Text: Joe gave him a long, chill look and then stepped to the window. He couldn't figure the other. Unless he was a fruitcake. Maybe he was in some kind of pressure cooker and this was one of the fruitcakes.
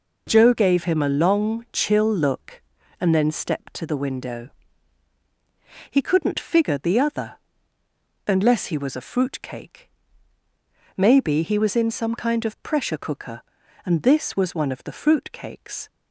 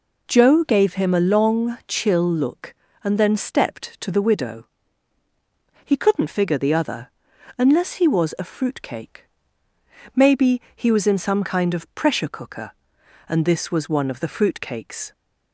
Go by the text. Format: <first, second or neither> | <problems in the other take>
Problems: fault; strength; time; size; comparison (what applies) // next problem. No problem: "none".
first | says "widow" for "window"; at 4.2 s